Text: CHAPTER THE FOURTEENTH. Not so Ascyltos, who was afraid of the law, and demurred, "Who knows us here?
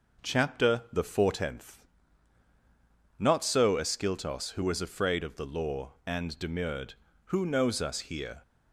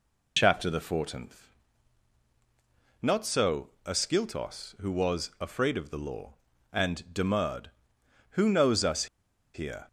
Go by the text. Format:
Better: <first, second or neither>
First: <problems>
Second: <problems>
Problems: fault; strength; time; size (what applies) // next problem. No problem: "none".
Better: first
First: none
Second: pauses between "so" and "Ascyltos"; slight; at 3.6 s; 0.18 s long // pauses between "us" and "here"; noticeable; at 9.0 s; 0.48 s long